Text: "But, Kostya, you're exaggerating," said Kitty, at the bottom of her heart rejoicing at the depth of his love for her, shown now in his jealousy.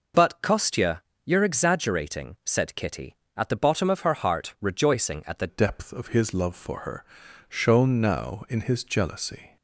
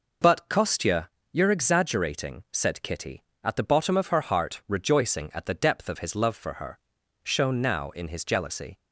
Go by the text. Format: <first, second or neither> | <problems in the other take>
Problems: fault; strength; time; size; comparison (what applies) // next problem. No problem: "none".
second | changes voice at "depth"; from 5.4 s on; 4.1 s long